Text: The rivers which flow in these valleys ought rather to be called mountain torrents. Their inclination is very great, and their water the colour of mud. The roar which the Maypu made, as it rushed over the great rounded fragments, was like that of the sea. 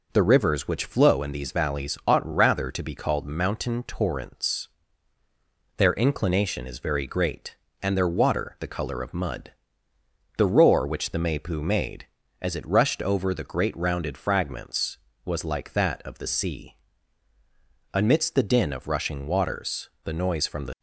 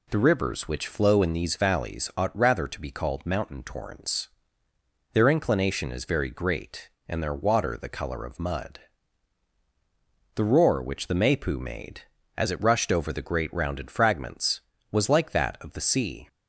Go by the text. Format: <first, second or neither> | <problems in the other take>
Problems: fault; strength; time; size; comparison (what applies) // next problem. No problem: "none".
second | goes on to say "Amidst the din of rushing waters the noise from the"; strong; from 17.9 s on; 2.8 s long